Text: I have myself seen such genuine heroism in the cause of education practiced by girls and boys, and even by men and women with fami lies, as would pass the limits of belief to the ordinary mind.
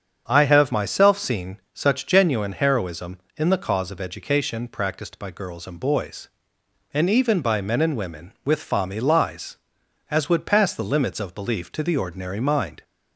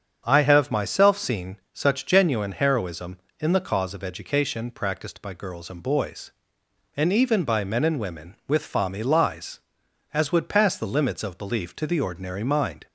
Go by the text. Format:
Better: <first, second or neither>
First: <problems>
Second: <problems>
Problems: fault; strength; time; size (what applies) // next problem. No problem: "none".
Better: neither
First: starts louder than the rest; strong; until 1.3 s; 7.5 dB // pauses between "seen" and "such"; slight; at 1.5 s; 0.16 s long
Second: starts louder than the rest; strong; until 1.2 s; 7.5 dB // pauses between "seen" and "such"; slight; at 1.5 s; 0.16 s long